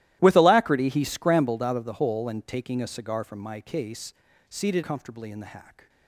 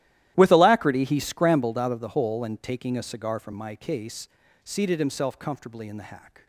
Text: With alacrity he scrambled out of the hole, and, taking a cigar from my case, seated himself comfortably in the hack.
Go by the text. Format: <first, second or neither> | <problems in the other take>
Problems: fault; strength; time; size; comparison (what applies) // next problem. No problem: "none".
second | starts louder than the rest; strong; until 1.2 s; 15.5 dB; strong in the second // skips "himself"; at 4.8 s